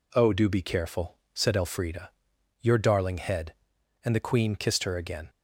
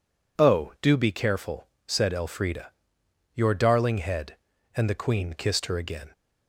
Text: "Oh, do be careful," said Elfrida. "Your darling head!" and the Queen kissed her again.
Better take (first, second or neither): neither